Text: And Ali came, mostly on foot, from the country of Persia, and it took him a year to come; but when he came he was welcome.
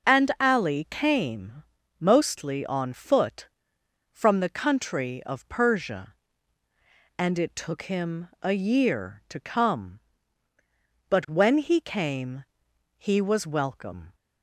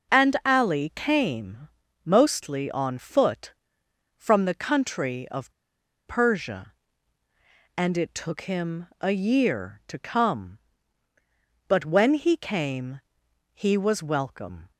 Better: first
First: pauses between "came" and "he"; noticeable; at 12.4 s; 0.54 s long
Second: pauses between "of" and "Persia"; noticeable; at 5.5 s; 0.53 s long // pauses between "came" and "he"; noticeable; at 13.0 s; 0.54 s long

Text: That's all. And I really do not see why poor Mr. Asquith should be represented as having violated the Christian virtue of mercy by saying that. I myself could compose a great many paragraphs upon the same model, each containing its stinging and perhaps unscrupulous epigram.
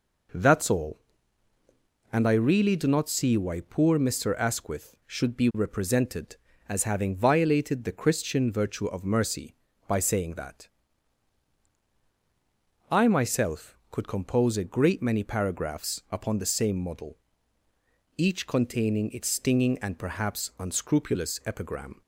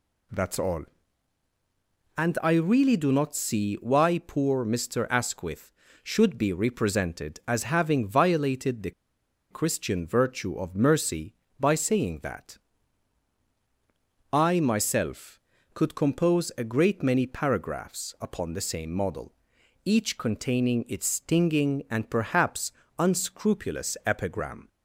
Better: first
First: none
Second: pauses between "the" and "Christian"; noticeable; at 8.9 s; 0.59 s long // pauses between "perhaps" and "unscrupulous"; slight; at 22.7 s; 0.26 s long

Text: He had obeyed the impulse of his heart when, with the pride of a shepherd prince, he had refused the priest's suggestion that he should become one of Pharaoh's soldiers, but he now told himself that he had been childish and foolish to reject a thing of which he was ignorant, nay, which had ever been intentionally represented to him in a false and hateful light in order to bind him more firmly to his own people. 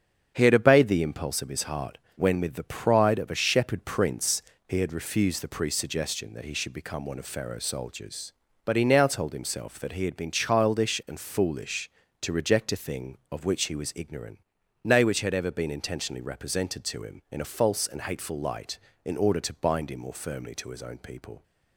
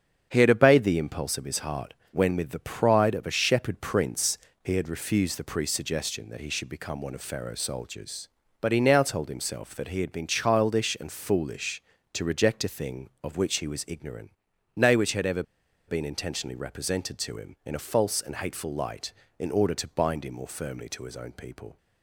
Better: first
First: starts louder than the rest; strong; until 1.3 s; 7.5 dB // pauses between "heart" and "when"; slight; at 1.9 s; 0.18 s long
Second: starts louder than the rest; strong; until 1.3 s; 7.5 dB // pauses between "heart" and "when"; slight; at 1.9 s; 0.18 s long // pauses between "ever" and "been"; at 15.4 s; 0.45 s long

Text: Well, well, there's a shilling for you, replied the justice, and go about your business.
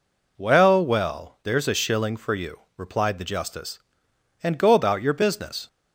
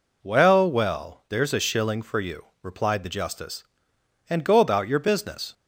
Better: neither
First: none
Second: none

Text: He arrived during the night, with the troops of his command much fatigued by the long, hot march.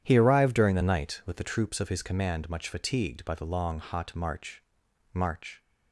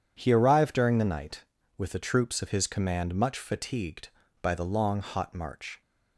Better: second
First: starts louder than the rest; strong; until 1.0 s; 10 dB // says "march" twice; at 5.1 s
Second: none

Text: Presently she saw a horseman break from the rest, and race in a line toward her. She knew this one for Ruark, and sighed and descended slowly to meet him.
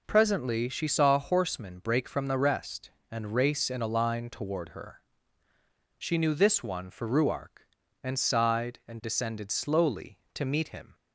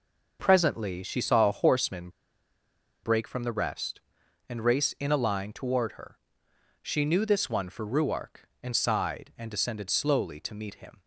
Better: first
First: none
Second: pauses between "horseman" and "break"; noticeable; at 2.0 s; 0.94 s long

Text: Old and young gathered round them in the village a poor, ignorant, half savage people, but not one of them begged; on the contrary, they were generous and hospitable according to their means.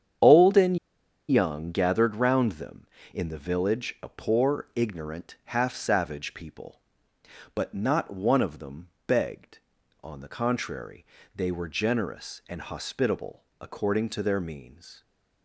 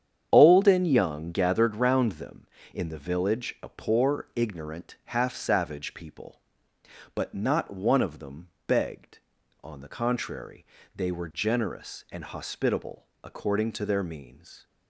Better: second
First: starts louder than the rest; strong; until 1.7 s; 8.5 dB // pauses between "and" and "young"; noticeable; at 0.7 s; 0.52 s long // pauses between "them" and "begged"; slight; at 8.9 s; 0.16 s long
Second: starts louder than the rest; strong; until 1.3 s; 8.5 dB // pauses between "them" and "begged"; slight; at 8.5 s; 0.16 s long

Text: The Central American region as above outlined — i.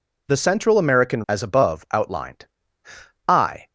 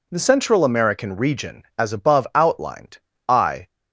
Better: second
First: skips "region"; at 1.2 s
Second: none

